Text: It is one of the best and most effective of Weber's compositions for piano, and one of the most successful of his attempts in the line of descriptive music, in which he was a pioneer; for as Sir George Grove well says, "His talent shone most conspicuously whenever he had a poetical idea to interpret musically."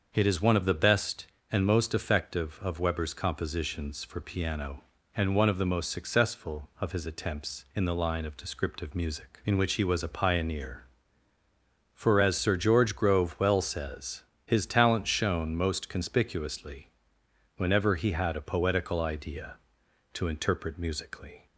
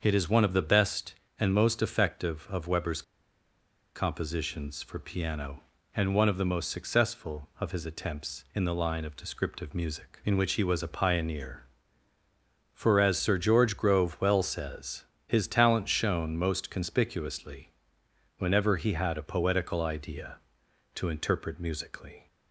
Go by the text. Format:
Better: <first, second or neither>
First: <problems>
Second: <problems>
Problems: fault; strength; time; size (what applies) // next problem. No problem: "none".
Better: first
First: starts louder than the rest; until 1.1 s; 6.5 dB // pauses between "conspicuously" and "whenever"; noticeable; at 16.8 s; 0.68 s long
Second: starts louder than the rest; until 1.0 s; 6.5 dB // pauses between "Weber's" and "compositions"; noticeable; at 3.0 s; 0.93 s long // pauses between "conspicuously" and "whenever"; noticeable; at 17.7 s; 0.68 s long